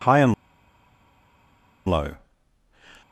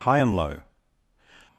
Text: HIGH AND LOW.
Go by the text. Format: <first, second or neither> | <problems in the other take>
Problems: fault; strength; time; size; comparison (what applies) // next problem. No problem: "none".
second | pauses between "AND" and "LOW"; strong; at 0.3 s; 1.5 s long